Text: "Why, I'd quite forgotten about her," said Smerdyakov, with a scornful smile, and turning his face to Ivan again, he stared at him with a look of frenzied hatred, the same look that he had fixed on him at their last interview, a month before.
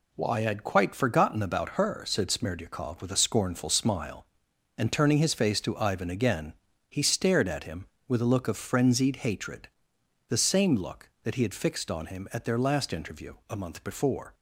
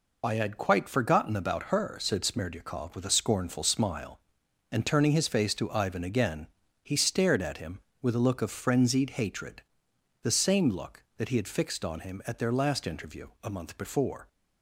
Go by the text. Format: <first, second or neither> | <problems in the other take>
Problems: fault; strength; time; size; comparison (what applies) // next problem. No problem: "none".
first | loses the start of "Why"; at 0.2 s; 160 ms